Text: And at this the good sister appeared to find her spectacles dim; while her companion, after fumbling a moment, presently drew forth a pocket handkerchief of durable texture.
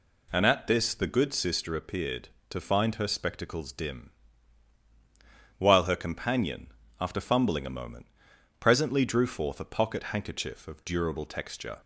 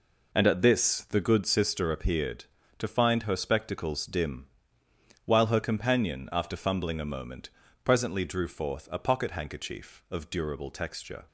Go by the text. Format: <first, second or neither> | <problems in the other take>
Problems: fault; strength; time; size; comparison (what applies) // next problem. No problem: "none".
neither | none